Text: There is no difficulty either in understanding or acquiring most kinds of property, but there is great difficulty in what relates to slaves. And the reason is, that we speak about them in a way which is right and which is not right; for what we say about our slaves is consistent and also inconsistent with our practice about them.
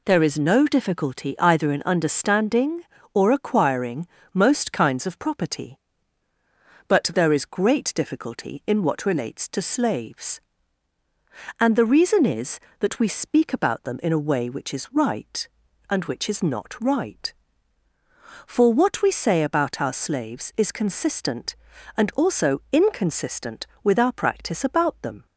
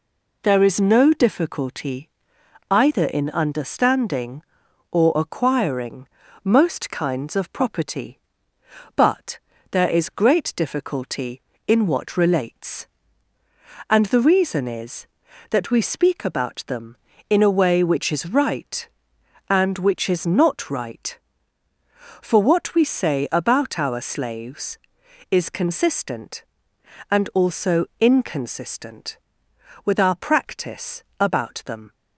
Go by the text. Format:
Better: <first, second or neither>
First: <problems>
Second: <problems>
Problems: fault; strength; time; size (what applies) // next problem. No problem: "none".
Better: first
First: pauses between "acquiring" and "most"; slight; at 4.0 s; 0.26 s long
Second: pauses between "difficulty" and "either"; noticeable; at 2.0 s; 0.62 s long // pauses between "acquiring" and "most"; slight; at 6.0 s; 0.34 s long // pauses between "but" and "there"; slight; at 9.3 s; 0.34 s long // skips "to slaves"; at 13.3 s // pauses between "practice" and "about"; slight; at 31.0 s; 0.16 s long